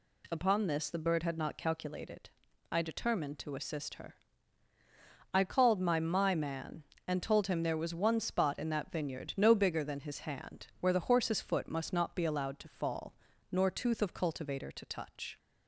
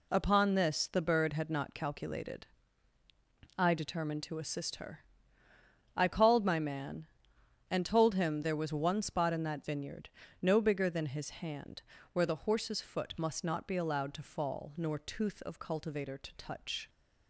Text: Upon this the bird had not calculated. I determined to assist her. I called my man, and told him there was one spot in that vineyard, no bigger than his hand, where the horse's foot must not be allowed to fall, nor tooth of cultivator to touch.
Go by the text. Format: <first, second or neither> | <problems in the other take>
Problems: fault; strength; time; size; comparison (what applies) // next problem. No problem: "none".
second | says "my" twice; at 5.9 s